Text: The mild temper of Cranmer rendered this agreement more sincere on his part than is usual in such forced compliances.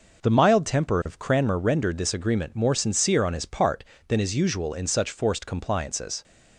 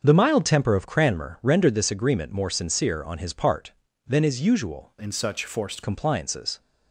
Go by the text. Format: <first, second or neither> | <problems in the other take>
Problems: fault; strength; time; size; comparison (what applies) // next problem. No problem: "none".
first | starts louder than the rest; until 1.0 s; 7 dB // changes voice from "in" to "forced"; from 4.9 to 5.8 s; 0.9 s long